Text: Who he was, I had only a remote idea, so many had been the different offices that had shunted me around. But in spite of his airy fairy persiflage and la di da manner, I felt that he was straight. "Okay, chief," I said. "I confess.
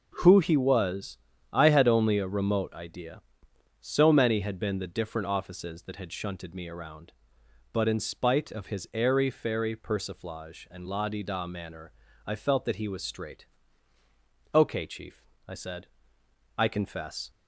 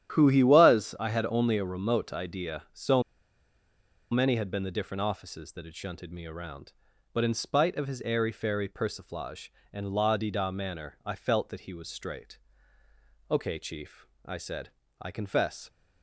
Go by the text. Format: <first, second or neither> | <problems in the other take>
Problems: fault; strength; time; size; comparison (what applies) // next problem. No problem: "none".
first | starts louder than the rest; strong; until 1.2 s; 10.5 dB // pauses between "so" and "many"; at 3.0 s; 1.1 s long